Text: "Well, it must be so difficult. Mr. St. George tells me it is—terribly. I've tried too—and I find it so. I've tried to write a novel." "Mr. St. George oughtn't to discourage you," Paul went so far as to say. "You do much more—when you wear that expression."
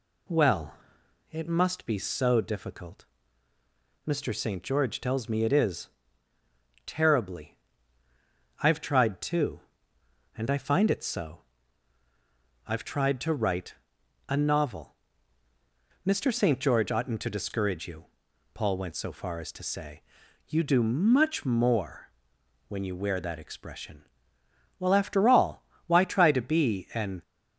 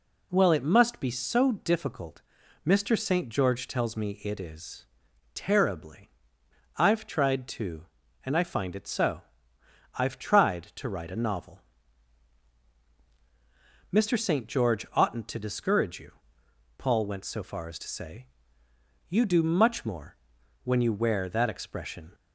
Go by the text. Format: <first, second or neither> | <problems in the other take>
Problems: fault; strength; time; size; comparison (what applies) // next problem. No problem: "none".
second | pauses between "write" and "a"; noticeable; at 13.7 s; 0.52 s long // goes on to say "Well after all why try to be an"; strong; from 24.7 s on; 2.4 s long